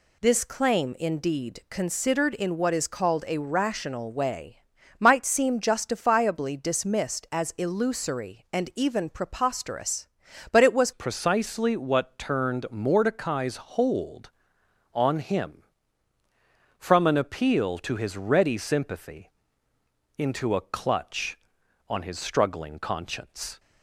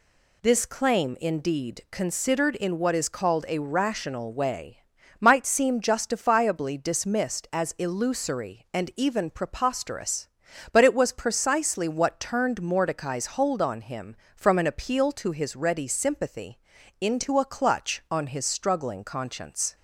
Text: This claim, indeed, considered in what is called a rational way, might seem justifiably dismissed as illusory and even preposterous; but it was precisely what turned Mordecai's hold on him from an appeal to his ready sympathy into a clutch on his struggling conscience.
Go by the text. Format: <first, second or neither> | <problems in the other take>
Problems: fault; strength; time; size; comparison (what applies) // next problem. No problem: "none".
second | changes voice at "precisely"; from 10.9 s on; 12.6 s long // pauses between "sympathy" and "into"; noticeable; at 19.3 s; 0.86 s long; also in the second